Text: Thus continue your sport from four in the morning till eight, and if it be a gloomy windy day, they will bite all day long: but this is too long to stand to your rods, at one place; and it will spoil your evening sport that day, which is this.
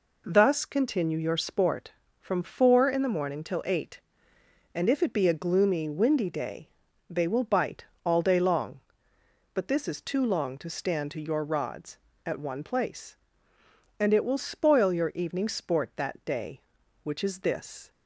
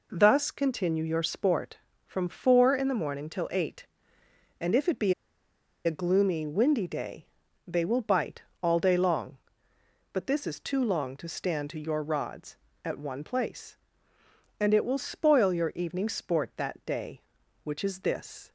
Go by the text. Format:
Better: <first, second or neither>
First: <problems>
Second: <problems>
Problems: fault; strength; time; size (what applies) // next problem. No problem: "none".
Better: first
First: pauses between "bite" and "all"; slight; at 7.8 s; 0.18 s long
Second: pauses between "be" and "a"; noticeable; at 5.1 s; 0.72 s long // pauses between "bite" and "all"; slight; at 8.4 s; 0.18 s long